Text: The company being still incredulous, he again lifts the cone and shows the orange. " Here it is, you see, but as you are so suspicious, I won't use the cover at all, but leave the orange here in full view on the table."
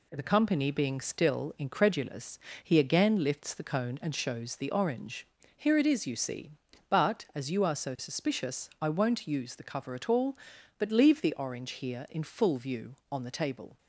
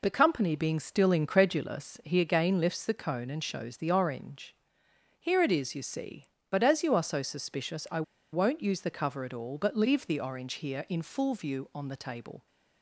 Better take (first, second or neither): first